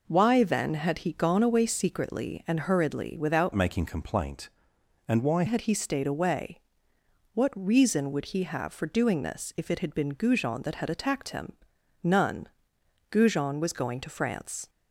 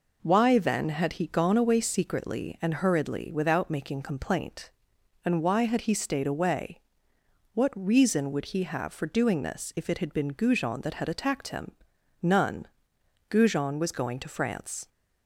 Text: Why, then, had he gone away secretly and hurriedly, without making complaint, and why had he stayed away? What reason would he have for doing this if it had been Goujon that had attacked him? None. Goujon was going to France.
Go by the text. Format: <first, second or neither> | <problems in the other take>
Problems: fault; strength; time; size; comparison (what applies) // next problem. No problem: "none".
second | changes voice from "making" to "why"; from 3.5 to 5.4 s; 1.9 s long